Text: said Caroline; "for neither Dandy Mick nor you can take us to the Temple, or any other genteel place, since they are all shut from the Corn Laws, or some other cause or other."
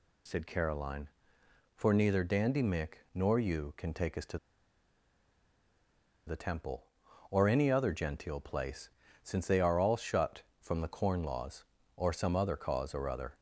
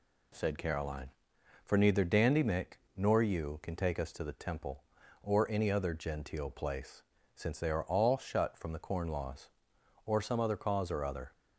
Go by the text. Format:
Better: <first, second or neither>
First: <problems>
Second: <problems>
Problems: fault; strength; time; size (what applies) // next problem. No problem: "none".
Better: second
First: pauses between "Mick" and "nor"; slight; at 2.9 s; 0.20 s long // pauses between "to" and "the"; strong; at 4.3 s; 1.9 s long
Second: pauses between "Mick" and "nor"; slight; at 2.7 s; 0.18 s long